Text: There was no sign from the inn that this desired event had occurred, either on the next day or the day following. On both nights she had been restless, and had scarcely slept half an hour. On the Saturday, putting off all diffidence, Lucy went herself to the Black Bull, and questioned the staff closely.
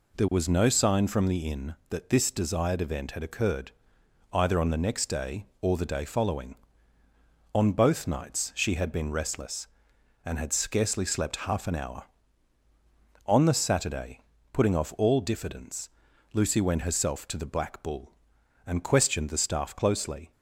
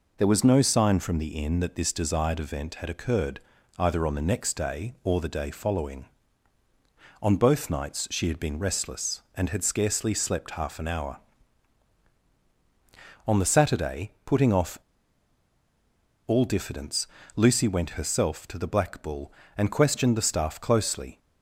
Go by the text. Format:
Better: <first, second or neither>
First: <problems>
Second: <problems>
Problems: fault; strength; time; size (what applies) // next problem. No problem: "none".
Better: first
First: none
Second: pauses between "off" and "all"; strong; at 14.7 s; 1.4 s long